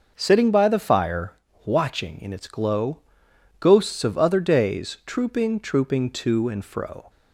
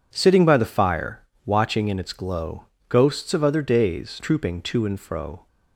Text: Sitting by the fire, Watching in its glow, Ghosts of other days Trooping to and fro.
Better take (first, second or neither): second